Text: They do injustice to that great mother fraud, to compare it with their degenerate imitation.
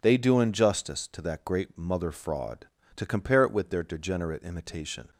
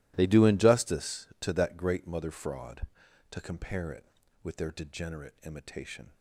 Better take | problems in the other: neither | none

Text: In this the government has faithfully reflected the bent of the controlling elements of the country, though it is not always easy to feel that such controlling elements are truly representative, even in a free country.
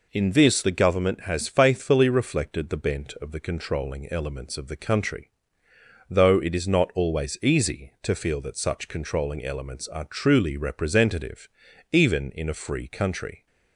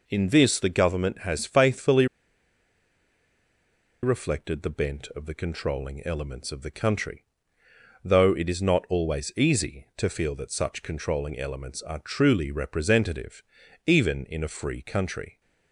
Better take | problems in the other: first | pauses between "faithfully" and "reflected"; strong; at 2.0 s; 1.9 s long

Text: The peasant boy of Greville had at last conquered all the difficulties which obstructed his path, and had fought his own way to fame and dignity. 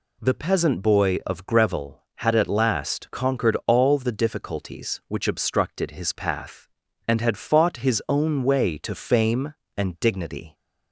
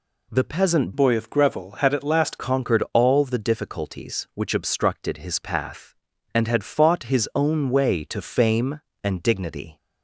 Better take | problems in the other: first | changes voice from "boy" to "last"; from 0.9 to 2.3 s; 1.4 s long

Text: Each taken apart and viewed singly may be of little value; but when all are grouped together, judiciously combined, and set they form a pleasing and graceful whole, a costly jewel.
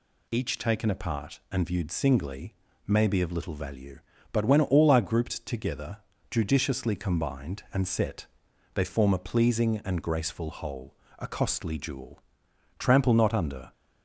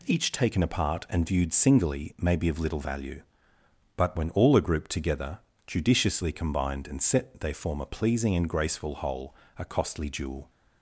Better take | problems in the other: second | pauses between "singly" and "may"; slight; at 2.5 s; 0.32 s long // pauses between "set" and "they"; noticeable; at 8.2 s; 0.48 s long // goes on to say "Trample not under"; noticeable; from 12.7 s on; 0.94 s long

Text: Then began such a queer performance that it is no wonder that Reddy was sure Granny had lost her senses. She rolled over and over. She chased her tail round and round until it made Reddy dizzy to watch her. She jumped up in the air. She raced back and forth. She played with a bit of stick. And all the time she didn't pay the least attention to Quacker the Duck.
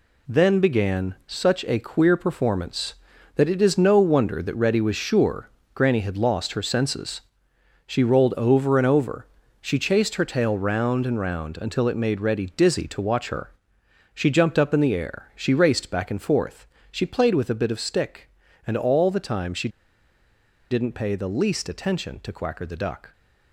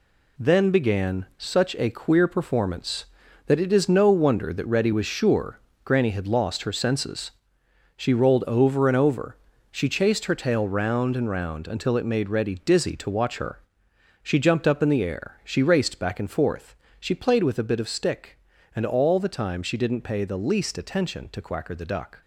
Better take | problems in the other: second | pauses between "sure" and "Granny"; slight; at 5.5 s; 0.24 s long; slight in the second // pauses between "she" and "didn't"; at 19.6 s; 1.0 s long

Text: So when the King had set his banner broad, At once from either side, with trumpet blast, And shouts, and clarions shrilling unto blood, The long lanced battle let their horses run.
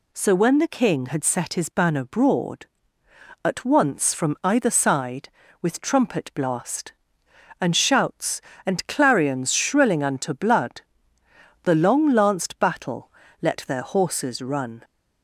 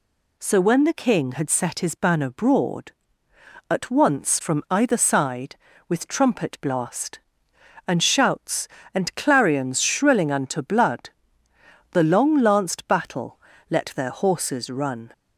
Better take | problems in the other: neither | pauses between "battle" and "let"; slight; the same in both

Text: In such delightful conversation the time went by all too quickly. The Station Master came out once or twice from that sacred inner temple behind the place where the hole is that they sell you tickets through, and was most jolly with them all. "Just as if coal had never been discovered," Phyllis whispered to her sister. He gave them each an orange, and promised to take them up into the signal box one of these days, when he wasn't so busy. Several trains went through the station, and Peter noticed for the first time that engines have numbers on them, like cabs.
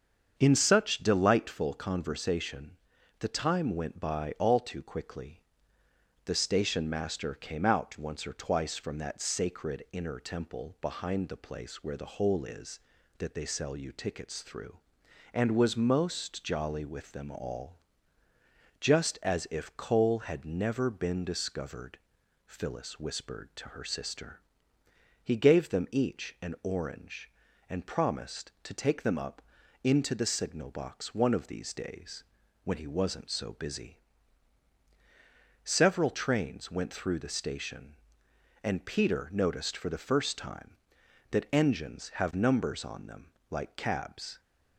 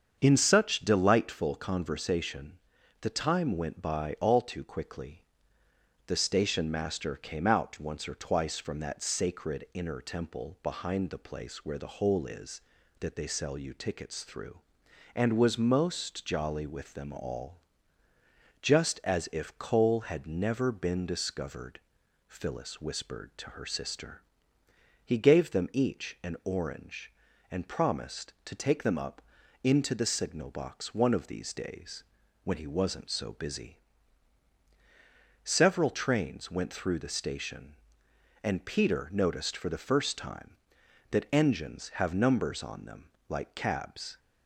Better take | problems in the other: neither | starts louder than the rest; strong; the same in both // pauses between "conversation" and "the"; noticeable; the same in both // pauses between "up" and "into"; the same in both

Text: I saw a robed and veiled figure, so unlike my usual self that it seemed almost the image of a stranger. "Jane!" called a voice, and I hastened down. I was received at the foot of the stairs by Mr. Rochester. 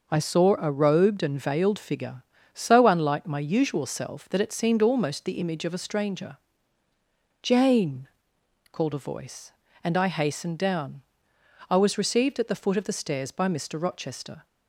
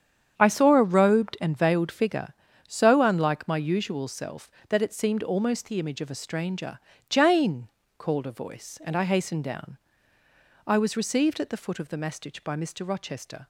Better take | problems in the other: first | starts louder than the rest; strong; until 1.3 s; 8 dB // says "mastich" for "stairs"; at 11.9 s

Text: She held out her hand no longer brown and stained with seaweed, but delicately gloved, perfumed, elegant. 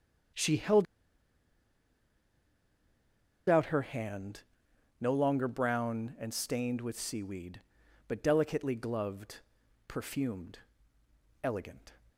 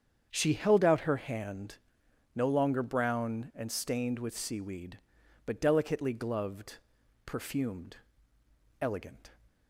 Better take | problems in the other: second | starts louder than the rest; strong; until 4.0 s; 7.5 dB; strong in the second // pauses between "held" and "out"; strong; at 0.8 s; 2.6 s long // pauses between "hand" and "no"; noticeable; at 4.4 s; 0.58 s long; noticeable in the second

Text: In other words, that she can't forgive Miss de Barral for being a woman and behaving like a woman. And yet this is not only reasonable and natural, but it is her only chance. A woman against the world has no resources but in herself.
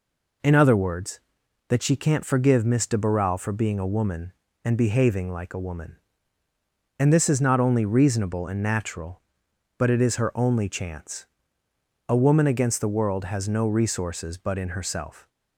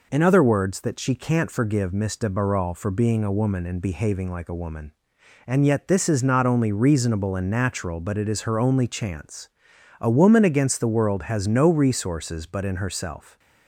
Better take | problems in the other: second | skips "yet"; at 7.1 s

